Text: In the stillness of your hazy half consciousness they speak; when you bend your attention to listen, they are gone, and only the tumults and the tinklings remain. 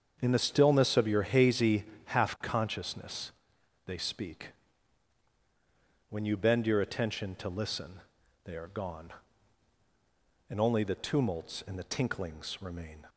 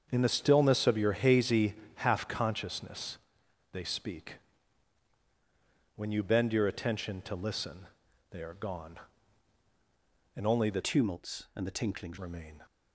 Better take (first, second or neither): first